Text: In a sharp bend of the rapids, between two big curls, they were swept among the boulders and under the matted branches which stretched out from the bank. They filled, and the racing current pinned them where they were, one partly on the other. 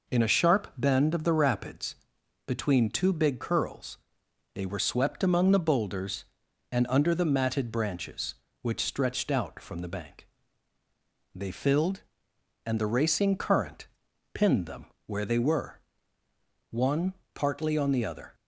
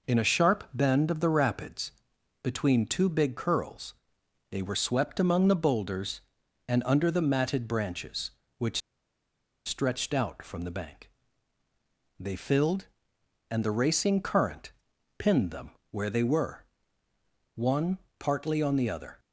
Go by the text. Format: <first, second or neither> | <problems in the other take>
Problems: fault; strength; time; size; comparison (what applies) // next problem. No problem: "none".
first | pauses between "which" and "stretched"; noticeable; at 8.8 s; 0.86 s long // pauses between "current" and "pinned"; noticeable; at 14.7 s; 0.48 s long; noticeable in the first // pauses between "them" and "where"; slight; at 15.7 s; 0.20 s long; slight in the first // pauses between "one" and "partly"; slight; at 17.9 s; 0.18 s long; slight in the first